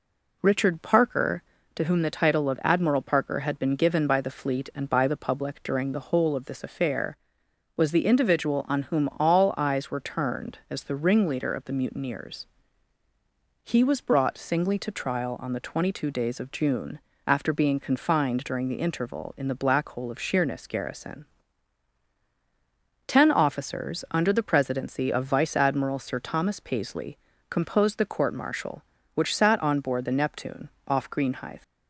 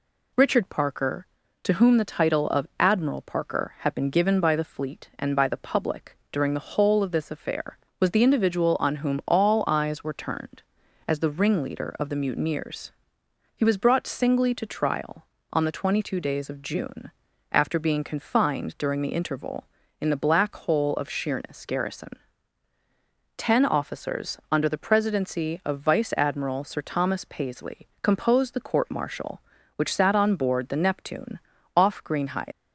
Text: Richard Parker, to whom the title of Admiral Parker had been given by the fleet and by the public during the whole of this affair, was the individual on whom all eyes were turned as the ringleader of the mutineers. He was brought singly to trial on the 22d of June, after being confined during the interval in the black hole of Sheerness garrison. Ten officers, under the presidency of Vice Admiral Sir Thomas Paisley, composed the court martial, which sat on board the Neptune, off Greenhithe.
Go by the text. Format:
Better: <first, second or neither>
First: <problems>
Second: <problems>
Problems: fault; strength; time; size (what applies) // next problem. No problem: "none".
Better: first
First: none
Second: leaves "Greenhithe" unfinished; at 32.5 s; 170 ms